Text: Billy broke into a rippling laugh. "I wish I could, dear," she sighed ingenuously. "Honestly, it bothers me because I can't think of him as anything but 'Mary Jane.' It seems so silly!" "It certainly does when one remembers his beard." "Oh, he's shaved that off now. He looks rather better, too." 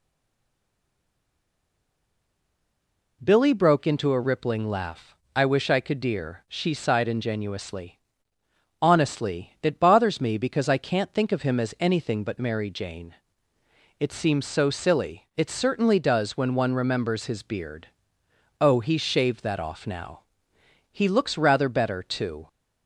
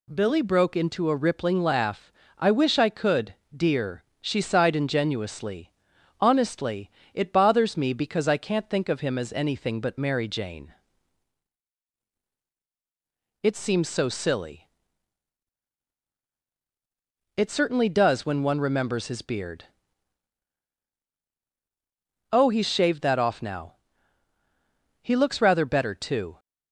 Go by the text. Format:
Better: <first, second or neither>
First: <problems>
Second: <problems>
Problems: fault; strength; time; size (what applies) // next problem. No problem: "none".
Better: second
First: stays silent before the first word; strong; until 3.2 s; 3.2 s long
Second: none